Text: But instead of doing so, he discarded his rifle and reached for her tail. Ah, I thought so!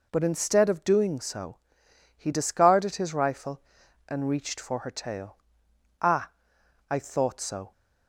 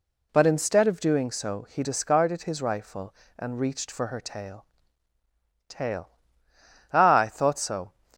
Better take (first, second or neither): first